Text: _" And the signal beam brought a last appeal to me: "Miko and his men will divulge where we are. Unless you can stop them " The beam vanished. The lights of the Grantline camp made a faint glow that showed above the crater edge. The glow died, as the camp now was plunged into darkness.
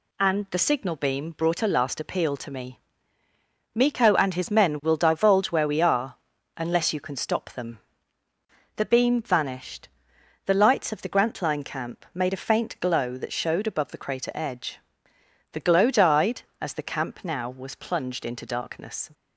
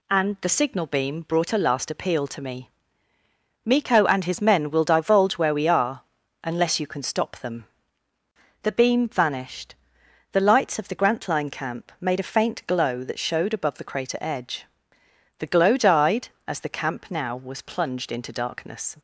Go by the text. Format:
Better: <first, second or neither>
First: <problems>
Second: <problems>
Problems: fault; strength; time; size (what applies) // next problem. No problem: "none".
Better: neither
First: none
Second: none